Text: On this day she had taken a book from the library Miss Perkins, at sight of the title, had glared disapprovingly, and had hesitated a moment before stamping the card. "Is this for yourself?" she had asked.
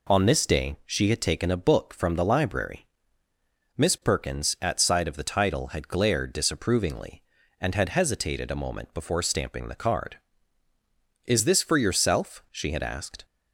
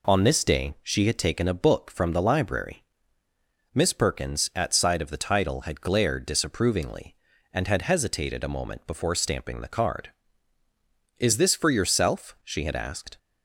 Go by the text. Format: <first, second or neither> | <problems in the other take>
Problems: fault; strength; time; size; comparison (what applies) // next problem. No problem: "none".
neither | pauses between "library" and "Miss"; noticeable; the same in both